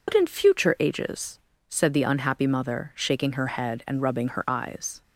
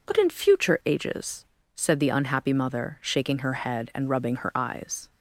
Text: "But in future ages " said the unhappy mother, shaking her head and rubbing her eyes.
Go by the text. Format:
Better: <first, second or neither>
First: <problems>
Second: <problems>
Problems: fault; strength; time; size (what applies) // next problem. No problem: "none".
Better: second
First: loses the start of "But"; at 0.0 s; 40 ms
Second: none